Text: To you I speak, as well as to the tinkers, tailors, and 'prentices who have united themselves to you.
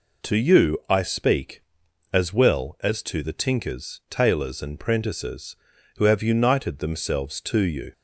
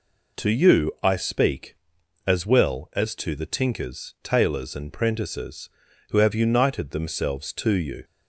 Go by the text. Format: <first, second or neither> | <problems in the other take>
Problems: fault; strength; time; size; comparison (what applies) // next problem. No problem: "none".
neither | none